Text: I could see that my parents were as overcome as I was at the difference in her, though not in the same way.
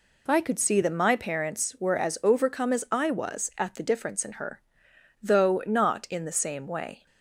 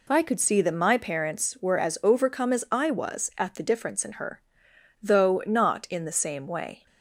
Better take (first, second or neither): neither